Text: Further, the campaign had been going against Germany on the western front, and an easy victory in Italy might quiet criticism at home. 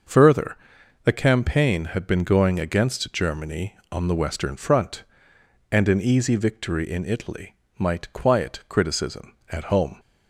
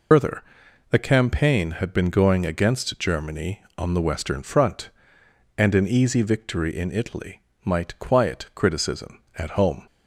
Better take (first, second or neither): first